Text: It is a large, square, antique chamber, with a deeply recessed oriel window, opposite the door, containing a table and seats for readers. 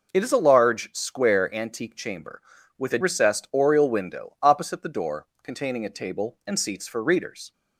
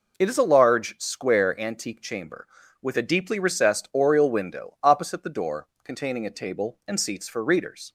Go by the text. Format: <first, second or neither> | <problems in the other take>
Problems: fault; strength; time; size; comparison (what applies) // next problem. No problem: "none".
second | skips "deeply"; at 2.9 s